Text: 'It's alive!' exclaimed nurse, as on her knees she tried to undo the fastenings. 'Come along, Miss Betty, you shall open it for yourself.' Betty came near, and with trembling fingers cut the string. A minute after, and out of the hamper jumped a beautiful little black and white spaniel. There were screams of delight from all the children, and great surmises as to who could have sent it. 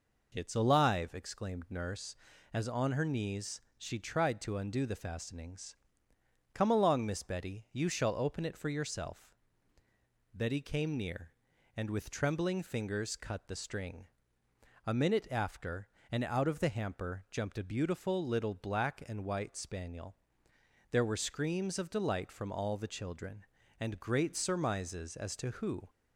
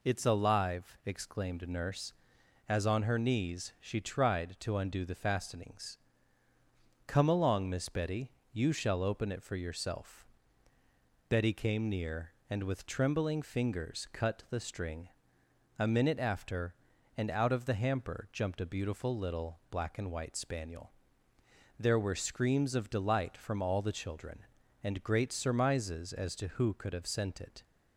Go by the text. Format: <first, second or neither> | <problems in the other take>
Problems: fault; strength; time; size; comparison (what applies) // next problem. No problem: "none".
second | pauses between "knees" and "she"; slight; at 3.6 s; 0.16 s long // stops before "could have sent it"; at 25.8 s